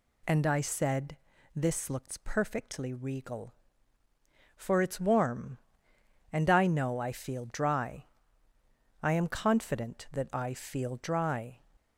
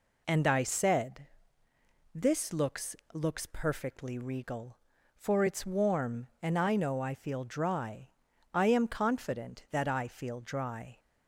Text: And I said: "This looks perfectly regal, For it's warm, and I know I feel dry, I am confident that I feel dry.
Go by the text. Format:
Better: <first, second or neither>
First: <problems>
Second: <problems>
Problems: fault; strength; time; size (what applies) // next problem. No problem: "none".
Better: first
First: none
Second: says "looks" twice; at 3.1 s